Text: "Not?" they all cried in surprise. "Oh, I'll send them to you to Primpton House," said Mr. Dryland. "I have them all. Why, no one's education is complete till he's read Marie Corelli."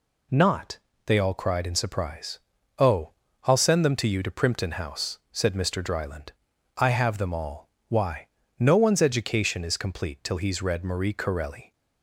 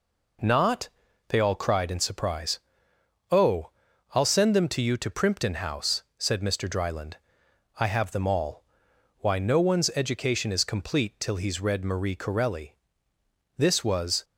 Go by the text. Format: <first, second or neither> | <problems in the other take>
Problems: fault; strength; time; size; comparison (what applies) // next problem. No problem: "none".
first | goes on to say "This was"; noticeable; from 13.5 s on; 0.66 s long